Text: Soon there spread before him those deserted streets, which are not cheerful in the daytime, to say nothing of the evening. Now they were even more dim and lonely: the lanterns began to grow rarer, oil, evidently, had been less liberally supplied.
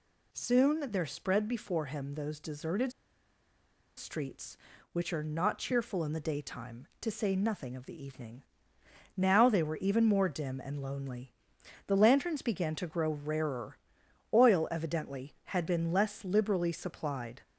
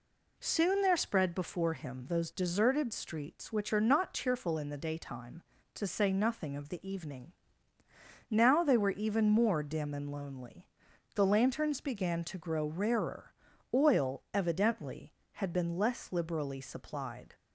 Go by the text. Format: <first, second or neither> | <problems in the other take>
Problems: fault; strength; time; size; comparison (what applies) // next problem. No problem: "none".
second | pauses between "deserted" and "streets"; at 2.9 s; 1.0 s long